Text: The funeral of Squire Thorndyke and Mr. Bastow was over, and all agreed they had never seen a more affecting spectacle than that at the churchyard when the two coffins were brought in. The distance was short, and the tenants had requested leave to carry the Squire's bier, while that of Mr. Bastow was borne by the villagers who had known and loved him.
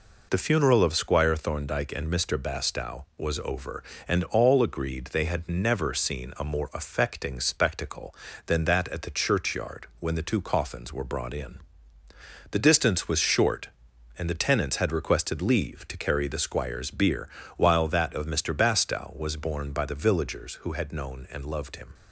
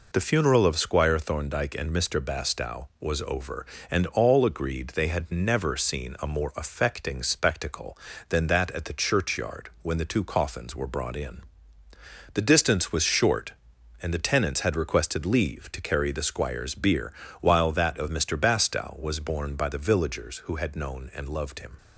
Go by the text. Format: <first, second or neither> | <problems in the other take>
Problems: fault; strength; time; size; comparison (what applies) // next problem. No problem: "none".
neither | none